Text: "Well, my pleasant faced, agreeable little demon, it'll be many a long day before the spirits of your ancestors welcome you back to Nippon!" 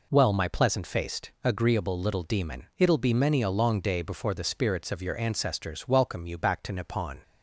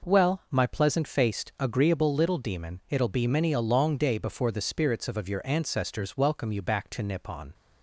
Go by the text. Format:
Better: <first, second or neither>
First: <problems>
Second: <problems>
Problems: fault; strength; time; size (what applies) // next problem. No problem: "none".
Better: first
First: none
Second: says "of" twice; at 5.1 s